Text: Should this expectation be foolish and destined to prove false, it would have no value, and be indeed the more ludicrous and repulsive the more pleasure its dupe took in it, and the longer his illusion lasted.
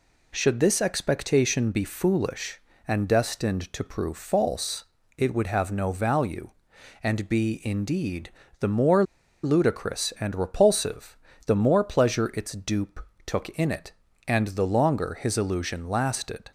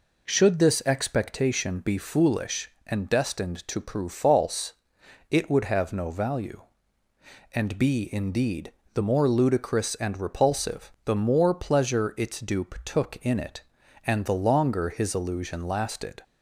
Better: second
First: pauses between "indeed" and "the"; slight; at 8.3 s; 0.26 s long // pauses between "more" and "ludicrous"; at 9.0 s; 0.39 s long // pauses between "repulsive" and "the"; slight; at 11.1 s; 0.28 s long // pauses between "dupe" and "took"; slight; at 13.0 s; 0.20 s long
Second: pauses between "indeed" and "the"; slight; at 8.7 s; 0.22 s long

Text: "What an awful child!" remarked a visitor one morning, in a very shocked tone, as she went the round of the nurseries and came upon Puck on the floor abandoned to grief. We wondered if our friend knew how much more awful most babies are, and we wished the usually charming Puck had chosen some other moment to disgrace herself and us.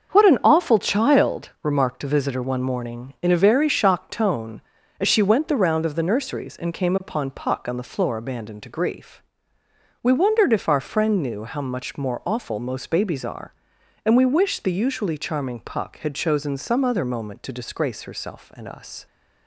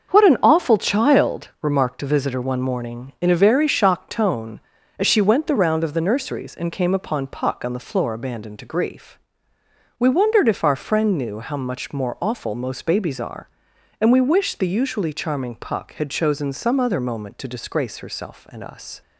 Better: neither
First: starts louder than the rest; until 1.1 s; 6.5 dB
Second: starts louder than the rest; until 1.1 s; 6.5 dB

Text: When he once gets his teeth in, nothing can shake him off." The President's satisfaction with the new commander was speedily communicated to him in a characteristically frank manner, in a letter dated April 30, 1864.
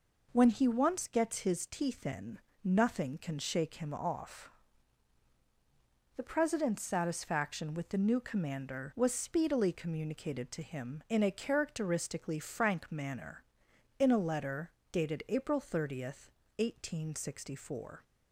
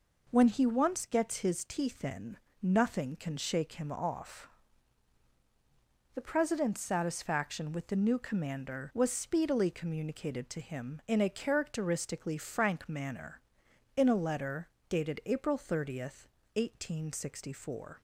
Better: neither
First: pauses between "letter" and "dated"; slight; at 14.6 s; 0.22 s long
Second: pauses between "letter" and "dated"; slight; at 14.6 s; 0.22 s long

